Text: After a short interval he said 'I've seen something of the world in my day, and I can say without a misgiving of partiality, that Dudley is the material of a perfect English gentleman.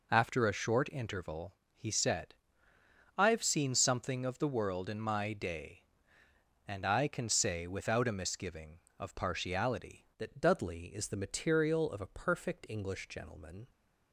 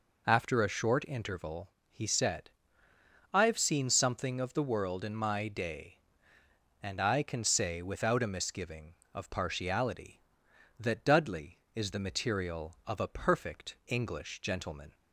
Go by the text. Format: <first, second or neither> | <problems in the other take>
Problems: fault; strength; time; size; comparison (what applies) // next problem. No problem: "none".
second | pauses between "interval" and "he"; slight; at 1.5 s; 0.20 s long; slight in the second // pauses between "said" and "I've"; noticeable; at 2.3 s; 0.86 s long; noticeable in the second // changes voice at "that"; from 10.1 s on; 3.5 s long